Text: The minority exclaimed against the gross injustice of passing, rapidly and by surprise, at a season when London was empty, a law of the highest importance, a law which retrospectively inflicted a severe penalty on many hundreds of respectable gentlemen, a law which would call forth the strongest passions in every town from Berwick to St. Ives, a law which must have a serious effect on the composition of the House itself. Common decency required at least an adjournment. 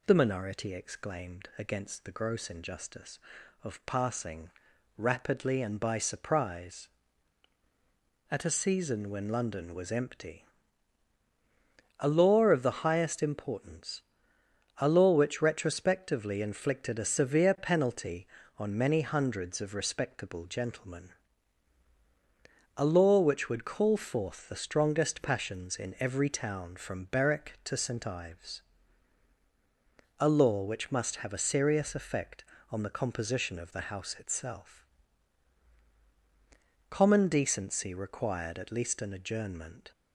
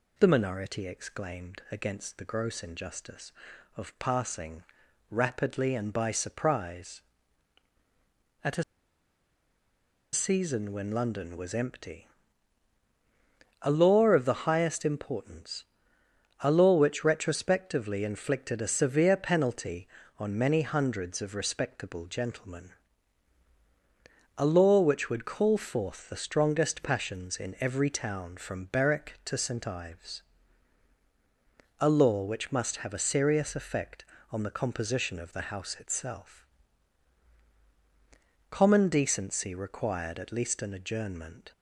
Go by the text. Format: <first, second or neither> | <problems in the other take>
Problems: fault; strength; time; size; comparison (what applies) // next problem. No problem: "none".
first | pauses between "a" and "season"; strong; at 8.6 s; 1.5 s long